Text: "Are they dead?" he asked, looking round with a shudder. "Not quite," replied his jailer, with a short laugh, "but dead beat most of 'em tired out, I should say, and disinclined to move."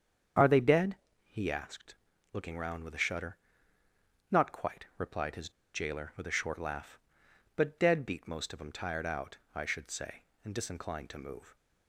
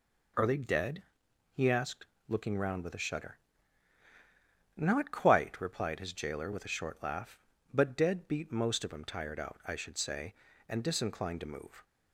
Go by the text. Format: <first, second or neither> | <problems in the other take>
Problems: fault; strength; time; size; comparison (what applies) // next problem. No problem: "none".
second | starts louder than the rest; strong; until 1.6 s; 7.5 dB // pauses between "his" and "jailer"; slight; at 5.4 s; 0.24 s long